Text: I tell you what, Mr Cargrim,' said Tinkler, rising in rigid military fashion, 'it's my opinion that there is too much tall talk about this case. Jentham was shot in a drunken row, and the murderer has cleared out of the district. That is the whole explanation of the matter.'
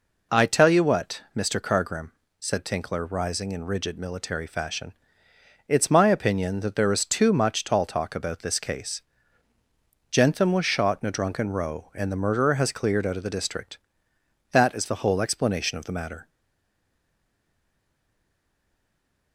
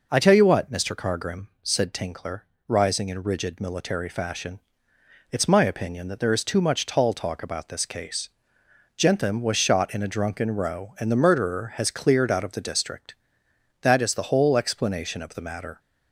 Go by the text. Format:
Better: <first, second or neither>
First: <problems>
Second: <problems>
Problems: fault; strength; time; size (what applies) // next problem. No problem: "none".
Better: second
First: stays silent after the last word; strong; from 16.2 s on; 3.1 s long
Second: none